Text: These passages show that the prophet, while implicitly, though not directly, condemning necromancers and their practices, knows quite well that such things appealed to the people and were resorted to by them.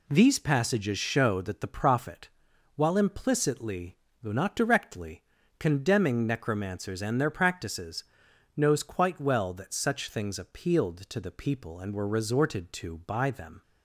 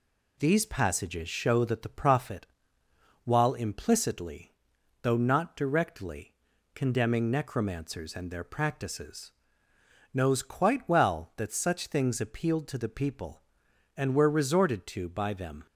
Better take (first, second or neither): neither